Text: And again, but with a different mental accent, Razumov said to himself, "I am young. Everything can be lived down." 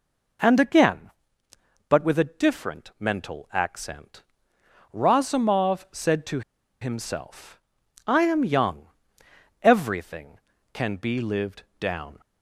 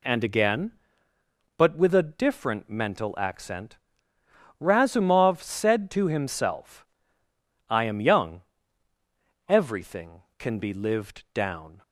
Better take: second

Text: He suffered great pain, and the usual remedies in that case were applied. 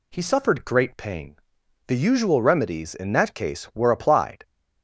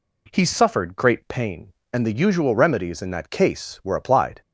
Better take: second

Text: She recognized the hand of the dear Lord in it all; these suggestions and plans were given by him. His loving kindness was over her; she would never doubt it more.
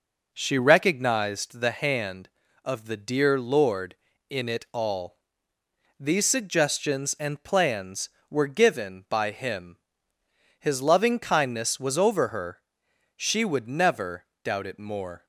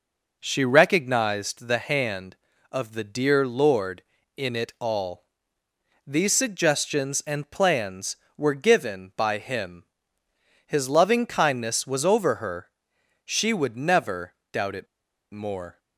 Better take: first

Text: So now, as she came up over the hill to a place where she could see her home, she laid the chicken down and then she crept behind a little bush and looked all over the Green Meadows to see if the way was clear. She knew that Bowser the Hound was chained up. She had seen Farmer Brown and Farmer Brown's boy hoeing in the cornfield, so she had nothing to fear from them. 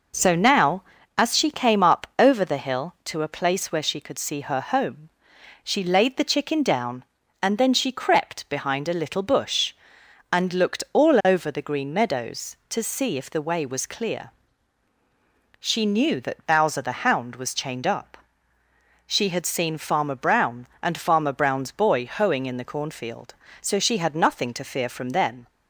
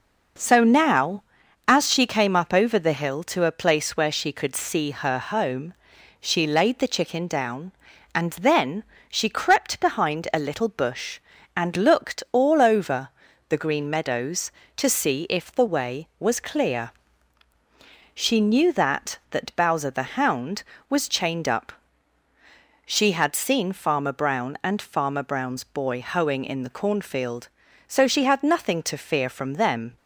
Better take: first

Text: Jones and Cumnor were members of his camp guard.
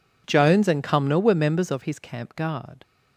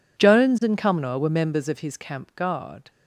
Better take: neither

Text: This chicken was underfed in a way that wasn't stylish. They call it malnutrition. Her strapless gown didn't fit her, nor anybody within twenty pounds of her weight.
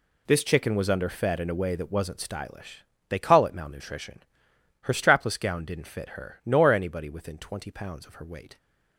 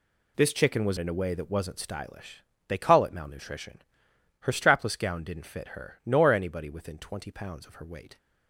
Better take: first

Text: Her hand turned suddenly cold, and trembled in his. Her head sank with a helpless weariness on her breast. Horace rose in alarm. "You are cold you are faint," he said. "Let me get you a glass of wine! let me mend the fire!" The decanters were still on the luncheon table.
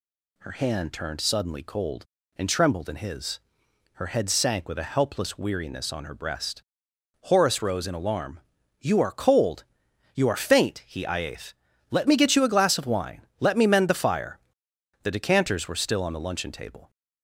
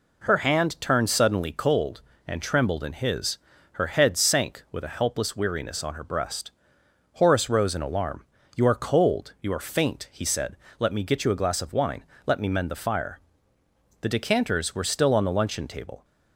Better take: second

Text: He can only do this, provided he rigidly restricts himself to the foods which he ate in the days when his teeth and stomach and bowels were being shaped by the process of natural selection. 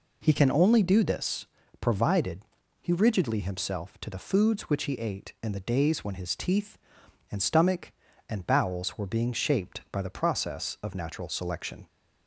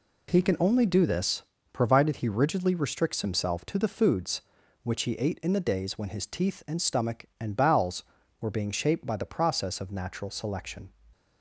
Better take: second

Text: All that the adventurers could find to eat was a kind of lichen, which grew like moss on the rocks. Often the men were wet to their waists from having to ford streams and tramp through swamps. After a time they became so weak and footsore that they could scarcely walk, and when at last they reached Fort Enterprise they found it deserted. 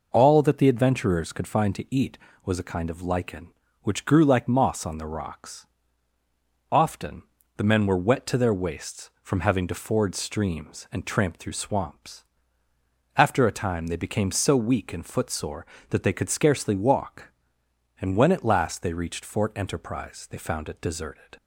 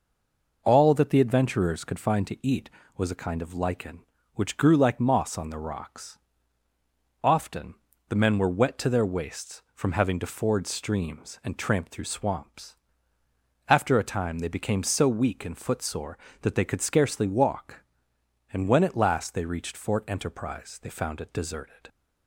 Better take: first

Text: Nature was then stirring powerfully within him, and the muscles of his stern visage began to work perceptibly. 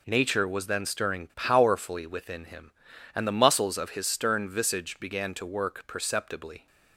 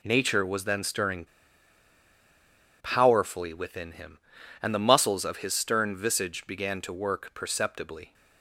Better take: first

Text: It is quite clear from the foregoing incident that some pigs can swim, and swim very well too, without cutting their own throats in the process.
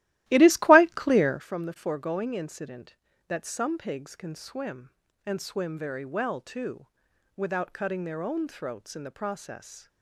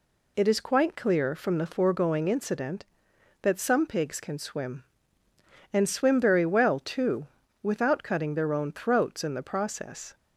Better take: second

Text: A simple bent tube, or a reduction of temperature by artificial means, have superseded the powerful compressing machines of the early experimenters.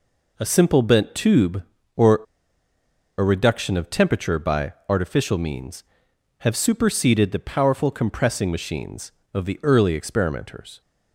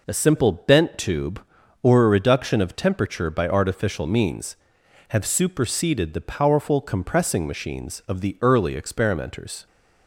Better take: second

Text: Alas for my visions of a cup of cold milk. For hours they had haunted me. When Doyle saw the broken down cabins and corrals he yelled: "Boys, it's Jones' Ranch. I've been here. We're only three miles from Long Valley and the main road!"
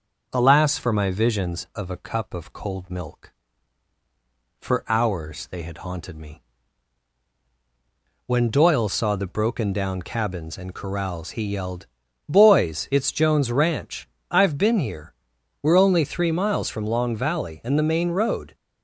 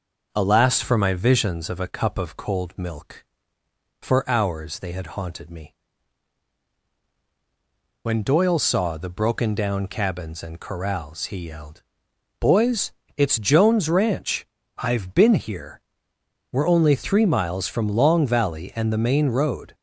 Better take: neither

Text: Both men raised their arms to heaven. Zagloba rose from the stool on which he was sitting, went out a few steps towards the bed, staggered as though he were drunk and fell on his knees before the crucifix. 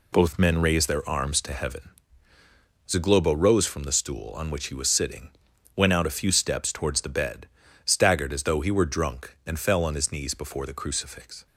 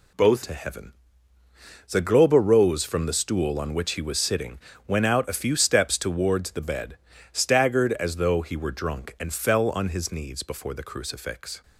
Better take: first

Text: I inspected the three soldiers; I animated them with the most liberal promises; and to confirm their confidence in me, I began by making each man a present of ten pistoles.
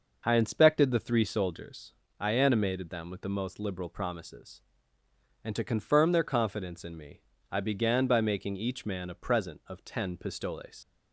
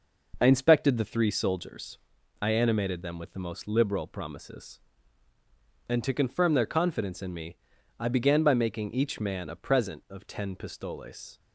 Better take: second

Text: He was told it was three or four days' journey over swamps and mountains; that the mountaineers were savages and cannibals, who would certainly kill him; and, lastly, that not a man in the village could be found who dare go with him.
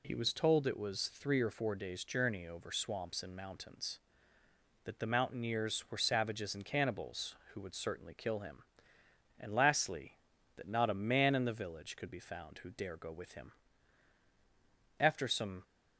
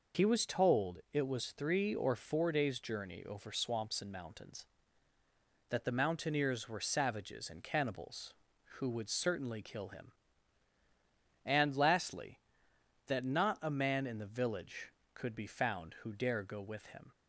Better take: second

